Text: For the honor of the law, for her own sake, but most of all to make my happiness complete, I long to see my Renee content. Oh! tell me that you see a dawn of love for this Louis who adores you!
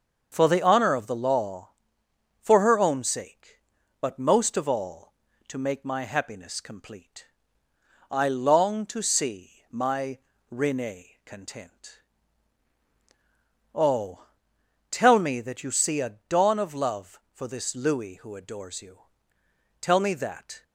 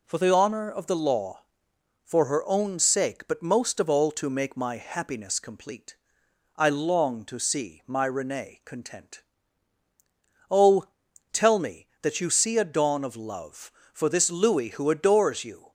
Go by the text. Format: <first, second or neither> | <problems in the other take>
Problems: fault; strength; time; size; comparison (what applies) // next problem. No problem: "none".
second | starts louder than the rest; until 1.3 s; 6.5 dB // pauses between "see" and "my"; slight; at 9.5 s; 0.20 s long // pauses between "my" and "Renee"; slight; at 10.1 s; 0.32 s long // goes on to say "Tell me that"; noticeable; from 19.8 s on; 0.82 s long